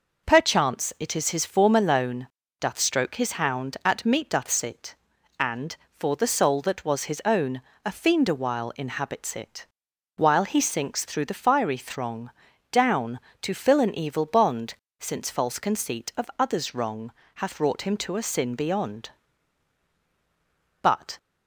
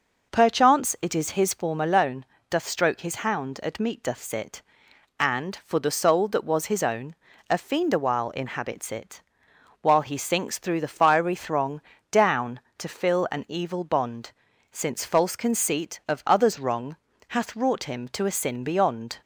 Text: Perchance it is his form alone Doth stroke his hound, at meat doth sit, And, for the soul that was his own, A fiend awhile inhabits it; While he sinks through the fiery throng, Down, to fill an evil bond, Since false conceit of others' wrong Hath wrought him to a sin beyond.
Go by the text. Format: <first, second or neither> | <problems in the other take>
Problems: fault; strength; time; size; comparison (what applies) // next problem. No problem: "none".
second | pauses between "alone" and "Doth"; slight; at 2.2 s; 0.34 s long; slight in the second // pauses between "wrong" and "Hath"; slight; at 17.1 s; 0.24 s long; slight in the second // goes on to say "But"; slight; from 20.8 s on; 0.36 s long